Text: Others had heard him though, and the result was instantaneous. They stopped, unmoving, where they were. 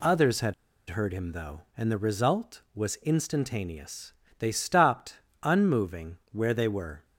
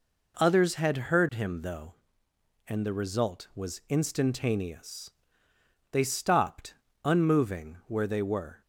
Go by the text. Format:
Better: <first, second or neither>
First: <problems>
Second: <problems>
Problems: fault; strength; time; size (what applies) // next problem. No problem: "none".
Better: second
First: pauses between "had" and "heard"; at 0.5 s; 0.36 s long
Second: none